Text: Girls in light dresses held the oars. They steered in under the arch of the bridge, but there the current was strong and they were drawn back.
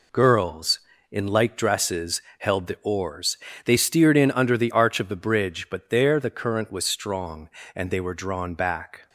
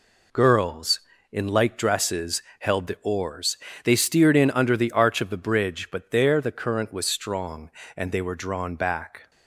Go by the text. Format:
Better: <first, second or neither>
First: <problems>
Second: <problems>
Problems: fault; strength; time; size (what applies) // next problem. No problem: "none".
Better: neither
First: pauses between "dresses" and "held"; slight; at 2.2 s; 0.18 s long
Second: pauses between "dresses" and "held"; slight; at 2.4 s; 0.18 s long